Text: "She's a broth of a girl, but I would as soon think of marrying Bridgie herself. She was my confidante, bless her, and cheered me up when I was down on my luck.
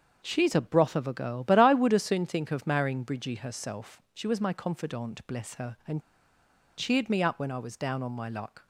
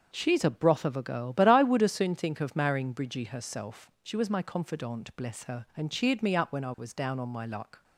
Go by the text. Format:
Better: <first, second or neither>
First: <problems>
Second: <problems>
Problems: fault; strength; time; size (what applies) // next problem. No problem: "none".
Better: second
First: starts louder than the rest; until 1.2 s; 6.5 dB // pauses between "and" and "cheered"; noticeable; at 6.0 s; 0.77 s long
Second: starts louder than the rest; until 1.1 s; 6.5 dB